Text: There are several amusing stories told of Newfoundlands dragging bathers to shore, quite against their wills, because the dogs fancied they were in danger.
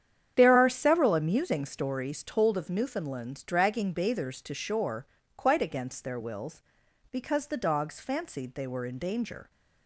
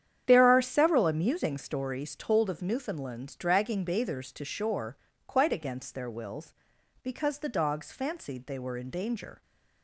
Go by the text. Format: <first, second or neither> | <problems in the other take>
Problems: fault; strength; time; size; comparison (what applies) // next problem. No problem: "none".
neither | starts louder than the rest; strong; the same in both